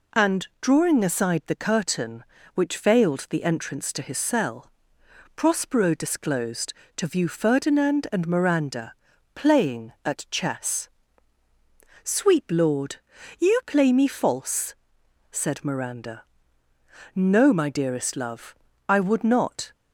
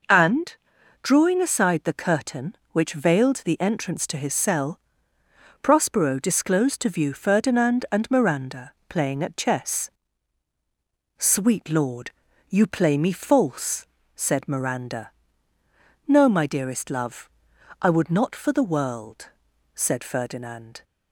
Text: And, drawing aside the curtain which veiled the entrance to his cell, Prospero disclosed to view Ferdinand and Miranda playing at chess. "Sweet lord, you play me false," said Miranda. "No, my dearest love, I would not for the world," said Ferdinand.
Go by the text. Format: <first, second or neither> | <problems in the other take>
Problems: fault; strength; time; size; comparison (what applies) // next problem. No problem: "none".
second | pauses between "Miranda" and "playing"; at 8.9 s; 0.40 s long; slight in the second // stops before "for the world said Ferdinand"; at 19.7 s